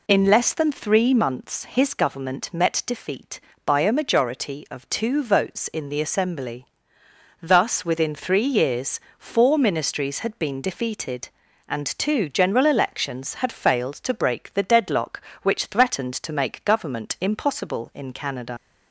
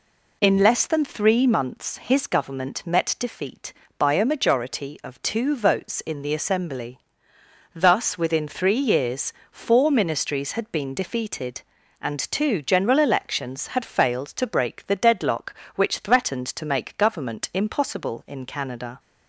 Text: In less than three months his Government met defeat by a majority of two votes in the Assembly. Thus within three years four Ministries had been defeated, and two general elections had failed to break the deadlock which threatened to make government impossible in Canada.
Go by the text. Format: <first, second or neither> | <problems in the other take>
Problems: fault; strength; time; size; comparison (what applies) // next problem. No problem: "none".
second | pauses between "years" and "four"; slight; at 8.9 s; 0.18 s long; slight in the second // leaves "Canada" unfinished; at 18.5 s; 90 ms